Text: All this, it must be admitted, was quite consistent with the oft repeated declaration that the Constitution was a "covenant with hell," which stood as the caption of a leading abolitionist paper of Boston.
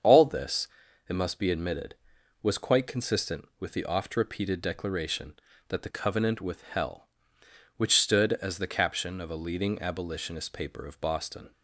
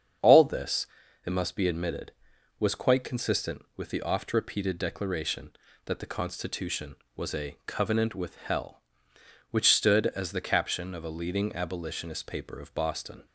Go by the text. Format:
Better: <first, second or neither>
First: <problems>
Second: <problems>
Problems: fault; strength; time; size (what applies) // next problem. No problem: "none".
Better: second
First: starts louder than the rest; strong; until 1.4 s; 7 dB // skips "Constitution was a"; at 5.9 s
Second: starts louder than the rest; strong; until 1.6 s; 7.5 dB